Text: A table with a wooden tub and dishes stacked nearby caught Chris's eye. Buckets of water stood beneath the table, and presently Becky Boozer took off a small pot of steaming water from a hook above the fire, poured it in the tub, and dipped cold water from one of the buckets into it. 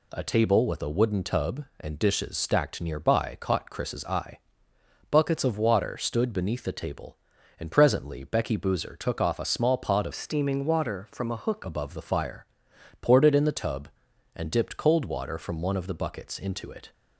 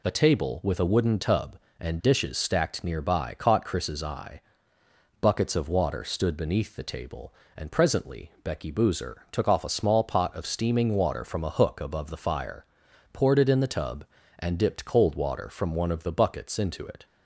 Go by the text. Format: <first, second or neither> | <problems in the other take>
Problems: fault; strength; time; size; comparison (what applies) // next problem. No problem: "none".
second | changes voice from "steaming" to "hook"; from 10.1 to 11.6 s; 1.5 s long